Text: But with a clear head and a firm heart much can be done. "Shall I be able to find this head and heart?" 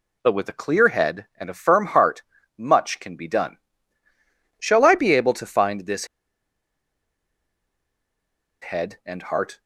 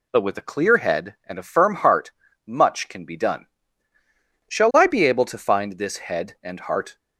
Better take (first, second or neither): second